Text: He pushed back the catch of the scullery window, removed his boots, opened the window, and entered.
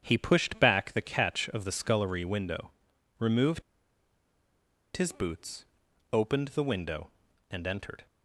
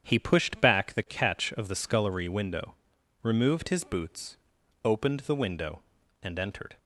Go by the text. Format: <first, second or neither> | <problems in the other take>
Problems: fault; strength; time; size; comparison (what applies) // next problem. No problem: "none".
second | starts louder than the rest; strong; until 1.0 s; 8.5 dB; strong in the second // pauses between "removed" and "his"; strong; at 3.6 s; 1.3 s long